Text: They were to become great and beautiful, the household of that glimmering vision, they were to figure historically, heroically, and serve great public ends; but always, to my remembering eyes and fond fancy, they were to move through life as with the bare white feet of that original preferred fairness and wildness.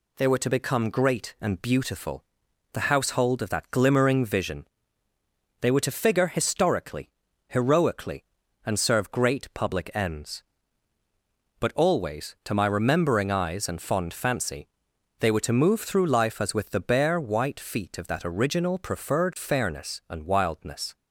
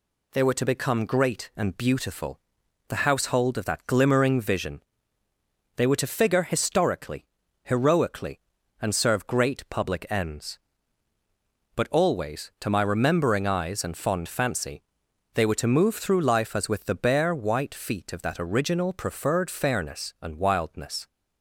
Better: neither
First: none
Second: none

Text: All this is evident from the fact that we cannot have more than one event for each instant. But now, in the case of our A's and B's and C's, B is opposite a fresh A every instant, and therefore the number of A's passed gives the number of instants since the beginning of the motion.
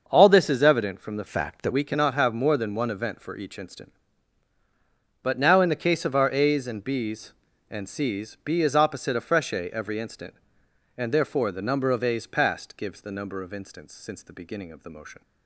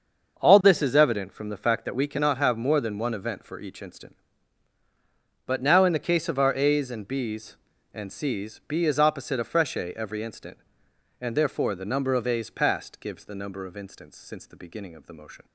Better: second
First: starts louder than the rest; until 1.0 s; 6.5 dB // changes voice from "fact" to "that"; from 1.2 to 1.7 s; 0.5 s long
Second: starts louder than the rest; until 1.4 s; 6.5 dB

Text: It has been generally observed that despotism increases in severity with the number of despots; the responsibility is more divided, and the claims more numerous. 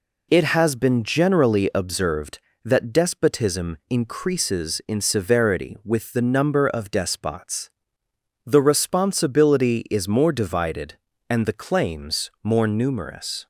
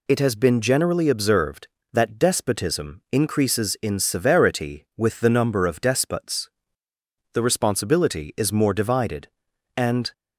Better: first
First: none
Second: stops before "the claims more numerous"; at 10.1 s

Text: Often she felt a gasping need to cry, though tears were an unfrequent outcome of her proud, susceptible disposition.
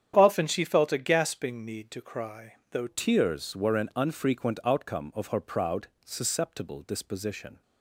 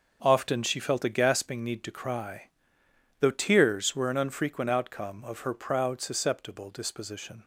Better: second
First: starts louder than the rest; strong; until 1.1 s; 9 dB // changes voice at "tears"; from 2.8 s on; 4.8 s long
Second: starts louder than the rest; until 1.2 s; 6 dB

